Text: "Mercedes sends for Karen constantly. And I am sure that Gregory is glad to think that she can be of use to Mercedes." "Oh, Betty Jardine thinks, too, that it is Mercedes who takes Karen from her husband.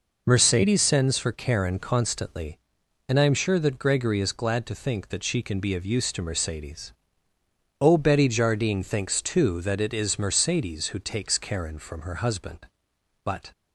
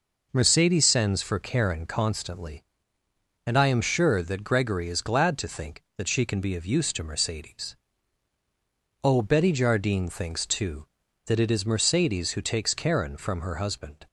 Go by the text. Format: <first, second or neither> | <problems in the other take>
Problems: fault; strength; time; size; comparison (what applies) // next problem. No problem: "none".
second | goes on to say "But"; slight; from 13.2 s on; 0.26 s long